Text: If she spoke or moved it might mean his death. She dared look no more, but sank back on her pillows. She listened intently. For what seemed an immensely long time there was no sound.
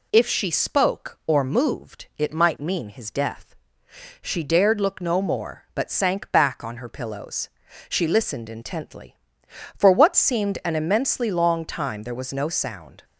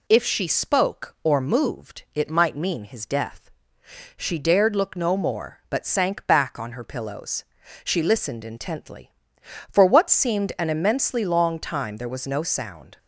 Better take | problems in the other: neither | none

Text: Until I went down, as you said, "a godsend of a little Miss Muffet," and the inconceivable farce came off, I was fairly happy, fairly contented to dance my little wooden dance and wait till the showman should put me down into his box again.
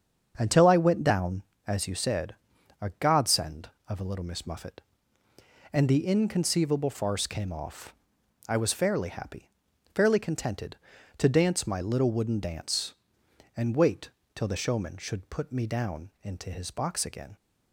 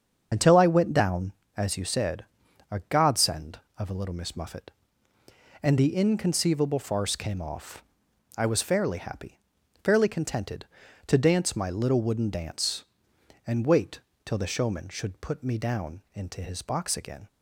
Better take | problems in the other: first | loses the start of "Until"; at 0.3 s; 70 ms // starts louder than the rest; until 1.3 s; 7 dB; also in the first // pauses between "wait" and "till"; slight; at 13.9 s; 0.26 s long; slight in the first

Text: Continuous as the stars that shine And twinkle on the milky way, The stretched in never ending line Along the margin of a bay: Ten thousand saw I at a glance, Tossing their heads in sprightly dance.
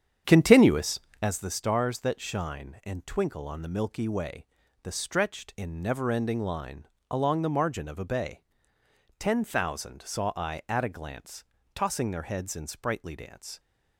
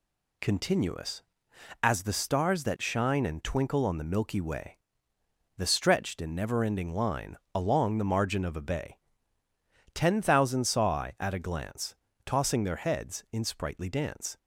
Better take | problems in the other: second | starts louder than the rest; strong; until 1.3 s; 8.5 dB // pauses between "line" and "Along"; slight; at 6.8 s; 0.24 s long; slight in the second

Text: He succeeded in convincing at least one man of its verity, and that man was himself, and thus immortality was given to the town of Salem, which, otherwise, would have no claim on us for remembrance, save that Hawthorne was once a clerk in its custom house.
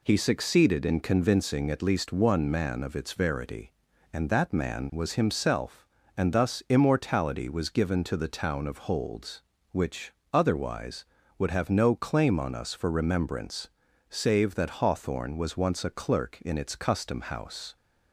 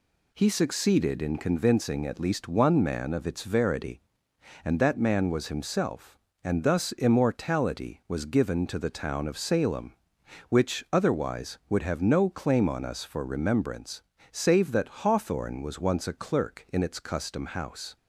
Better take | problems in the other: second | says "Holds" for "Salem"; at 8.7 s

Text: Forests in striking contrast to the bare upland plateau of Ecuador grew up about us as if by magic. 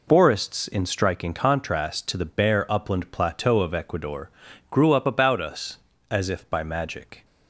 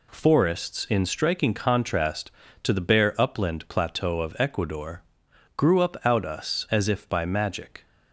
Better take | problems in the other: first | pauses between "Ecuador" and "grew"; noticeable; at 5.0 s; 0.54 s long; also in the first // says "out" for "about"; at 6.0 s

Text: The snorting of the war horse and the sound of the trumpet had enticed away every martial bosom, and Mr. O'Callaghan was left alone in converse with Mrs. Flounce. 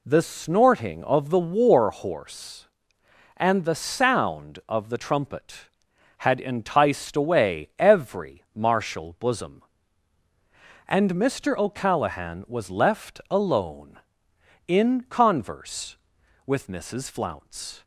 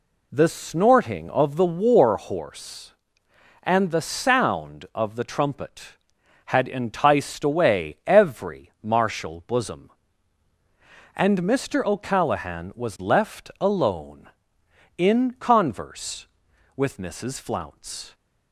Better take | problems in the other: neither | none

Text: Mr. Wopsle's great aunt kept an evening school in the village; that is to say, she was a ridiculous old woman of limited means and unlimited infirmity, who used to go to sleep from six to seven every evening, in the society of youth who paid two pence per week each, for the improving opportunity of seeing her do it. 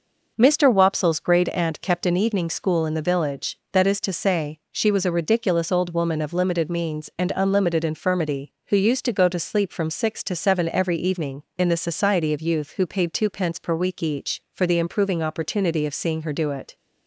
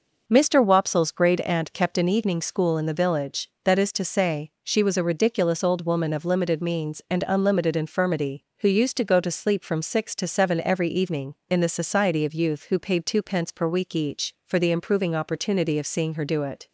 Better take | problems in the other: neither | none

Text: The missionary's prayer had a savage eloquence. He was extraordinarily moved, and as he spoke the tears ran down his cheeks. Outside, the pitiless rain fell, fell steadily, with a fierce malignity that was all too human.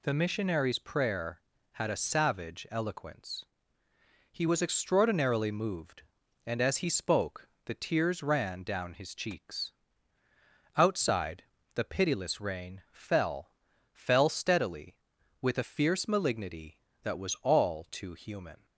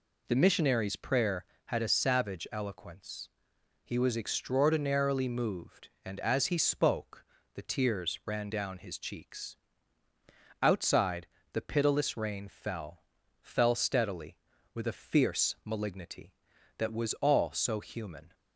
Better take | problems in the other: first | pauses between "spoke" and "the"; slight; at 7.2 s; 0.30 s long; slight in the first // says "so" for "too"; at 17.5 s

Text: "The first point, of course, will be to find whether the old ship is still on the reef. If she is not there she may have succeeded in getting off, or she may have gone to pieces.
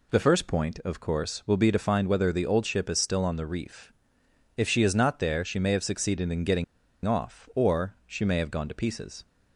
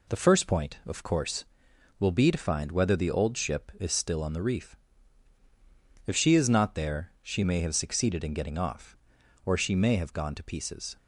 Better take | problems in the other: second | pauses between "getting" and "off"; at 6.6 s; 0.40 s long

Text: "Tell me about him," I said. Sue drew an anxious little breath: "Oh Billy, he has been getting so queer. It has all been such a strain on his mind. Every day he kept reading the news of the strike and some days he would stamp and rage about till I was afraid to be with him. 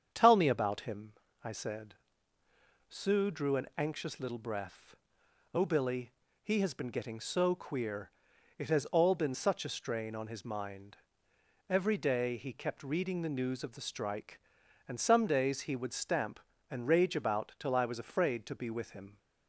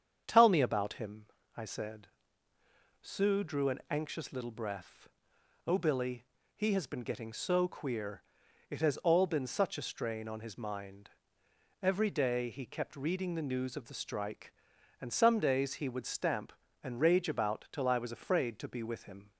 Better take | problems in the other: neither | starts louder than the rest; strong; the same in both

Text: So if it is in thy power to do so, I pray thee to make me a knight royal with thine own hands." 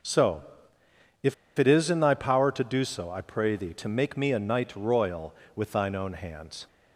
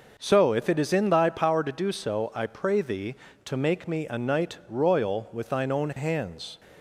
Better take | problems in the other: second | starts louder than the rest; until 2.0 s; 6.5 dB // pauses between "So" and "if"; noticeable; at 0.4 s; 0.82 s long // pauses between "if" and "it"; slight; at 1.3 s; 0.24 s long

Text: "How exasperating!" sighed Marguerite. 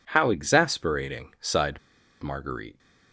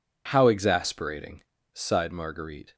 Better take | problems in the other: second | pauses between "sighed" and "Marguerite"; at 1.7 s; 0.43 s long

